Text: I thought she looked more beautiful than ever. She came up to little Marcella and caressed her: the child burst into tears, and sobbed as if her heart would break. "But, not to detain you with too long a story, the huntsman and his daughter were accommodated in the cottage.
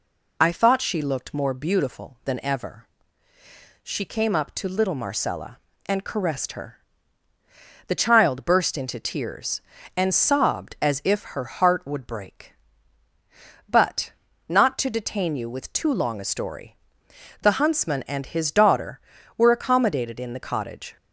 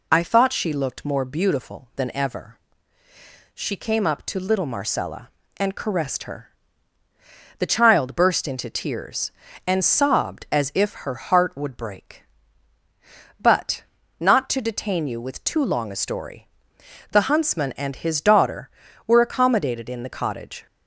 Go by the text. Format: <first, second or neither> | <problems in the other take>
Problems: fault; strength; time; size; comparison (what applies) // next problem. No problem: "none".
neither | none